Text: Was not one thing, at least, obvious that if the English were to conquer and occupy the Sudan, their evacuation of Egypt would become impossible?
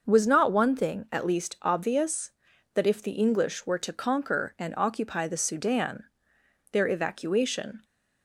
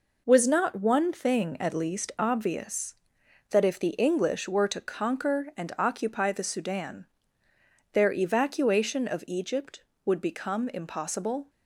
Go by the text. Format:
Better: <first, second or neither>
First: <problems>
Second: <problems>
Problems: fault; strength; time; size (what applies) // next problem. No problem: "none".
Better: second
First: starts louder than the rest; noticeable; until 1.0 s; 6 dB // stops before "of Egypt would become impossible"; at 7.8 s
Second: none